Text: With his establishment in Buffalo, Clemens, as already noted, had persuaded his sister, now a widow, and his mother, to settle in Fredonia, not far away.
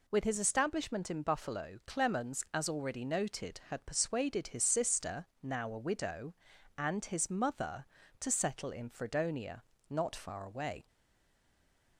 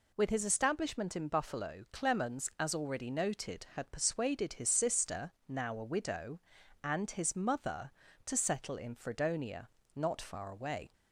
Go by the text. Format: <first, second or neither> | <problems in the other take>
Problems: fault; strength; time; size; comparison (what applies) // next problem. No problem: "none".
second | stays silent after the last word; from 10.8 s on; 1.1 s long